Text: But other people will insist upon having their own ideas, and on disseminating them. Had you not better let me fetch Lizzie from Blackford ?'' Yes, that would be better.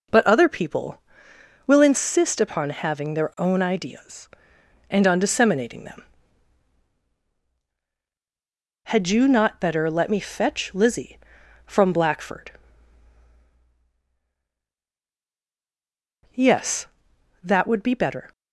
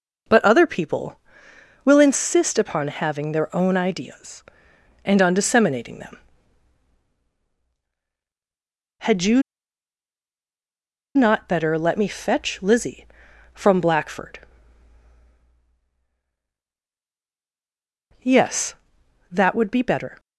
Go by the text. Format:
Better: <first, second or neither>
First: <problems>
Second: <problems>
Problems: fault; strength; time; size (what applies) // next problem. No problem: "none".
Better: first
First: none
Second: pauses between "you" and "not"; strong; at 9.4 s; 1.7 s long